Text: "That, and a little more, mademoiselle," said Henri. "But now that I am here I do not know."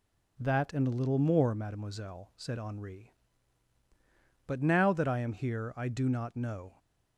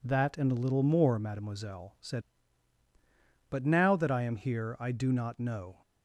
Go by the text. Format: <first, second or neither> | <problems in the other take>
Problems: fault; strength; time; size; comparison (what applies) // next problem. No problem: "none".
first | skips "Henri"; at 2.8 s